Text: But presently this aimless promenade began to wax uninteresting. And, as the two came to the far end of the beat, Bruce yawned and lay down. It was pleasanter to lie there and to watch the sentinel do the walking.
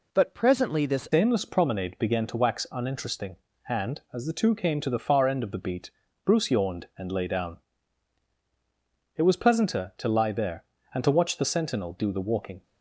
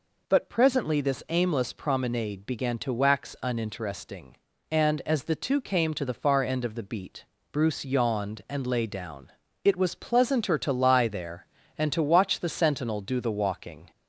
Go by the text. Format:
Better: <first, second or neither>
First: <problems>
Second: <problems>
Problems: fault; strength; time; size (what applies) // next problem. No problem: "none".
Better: second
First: changes voice at "aimless"; from 1.1 s on; 11.5 s long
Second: none